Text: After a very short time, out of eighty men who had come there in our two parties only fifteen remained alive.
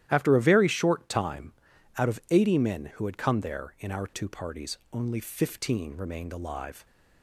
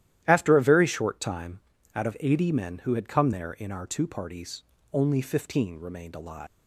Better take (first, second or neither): first